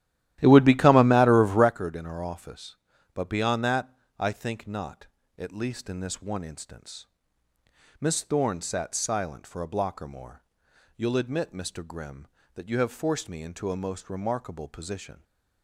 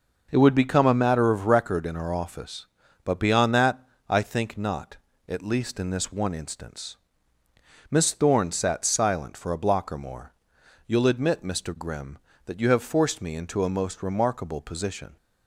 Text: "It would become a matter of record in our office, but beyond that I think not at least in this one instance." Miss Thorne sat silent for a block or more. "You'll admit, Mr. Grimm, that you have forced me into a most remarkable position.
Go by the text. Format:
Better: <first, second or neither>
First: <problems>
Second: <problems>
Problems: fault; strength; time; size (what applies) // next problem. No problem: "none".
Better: second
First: starts louder than the rest; strong; until 1.7 s; 13.5 dB // pauses between "that" and "I"; slight; at 3.9 s; 0.24 s long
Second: pauses between "that" and "I"; slight; at 3.8 s; 0.24 s long